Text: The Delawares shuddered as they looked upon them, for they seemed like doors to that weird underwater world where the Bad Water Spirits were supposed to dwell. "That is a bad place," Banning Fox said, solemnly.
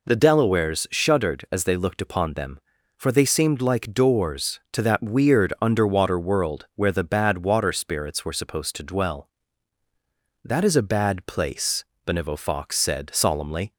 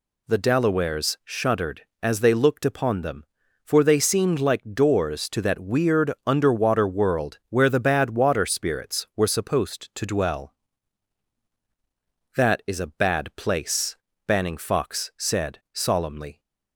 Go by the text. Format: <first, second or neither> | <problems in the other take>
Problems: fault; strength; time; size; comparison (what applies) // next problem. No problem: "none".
second | says "Benevo" for "Banning"; at 12.0 s